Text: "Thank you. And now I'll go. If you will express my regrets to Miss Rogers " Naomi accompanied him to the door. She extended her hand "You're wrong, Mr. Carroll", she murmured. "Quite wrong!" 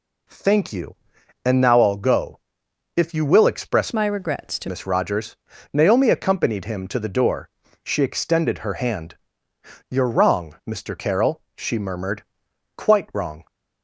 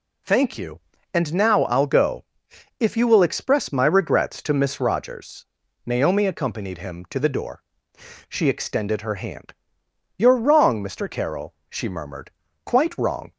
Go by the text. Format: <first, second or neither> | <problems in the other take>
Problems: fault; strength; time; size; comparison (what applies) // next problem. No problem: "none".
second | changes voice from "my" to "to"; from 3.9 to 4.6 s; 0.7 s long // pauses between "hand" and "You're"; noticeable; at 9.1 s; 0.74 s long; noticeable in the second